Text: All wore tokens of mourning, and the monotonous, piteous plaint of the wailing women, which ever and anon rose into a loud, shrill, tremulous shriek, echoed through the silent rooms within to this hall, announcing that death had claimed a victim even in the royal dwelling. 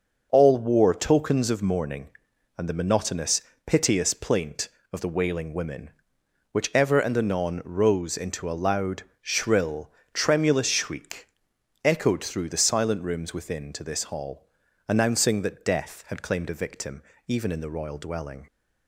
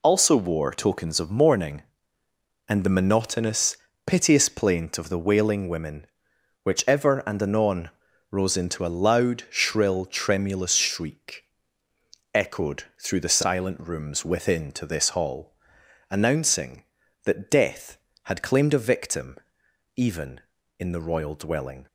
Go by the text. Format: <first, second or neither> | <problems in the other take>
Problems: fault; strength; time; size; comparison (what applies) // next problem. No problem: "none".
first | says "Also" for "All"; at 0.0 s // pauses between "anon" and "rose"; at 7.8 s; 0.42 s long // pauses between "echoed" and "through"; slight; at 12.8 s; 0.20 s long // pauses between "victim" and "even"; noticeable; at 19.3 s; 0.62 s long; slight in the first